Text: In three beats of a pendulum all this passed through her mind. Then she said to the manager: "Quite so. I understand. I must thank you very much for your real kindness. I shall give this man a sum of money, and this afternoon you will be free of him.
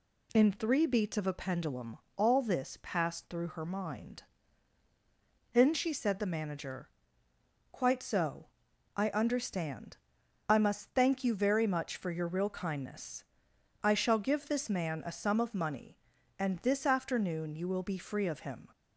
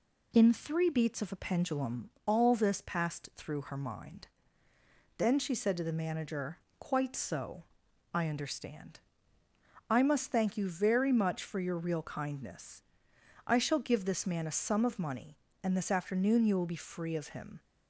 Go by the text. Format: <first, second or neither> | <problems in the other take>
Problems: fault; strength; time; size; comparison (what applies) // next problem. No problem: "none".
second | pauses between "pendulum" and "all"; slight; at 1.9 s; 0.20 s long; slight in the second // skips "to"; at 6.2 s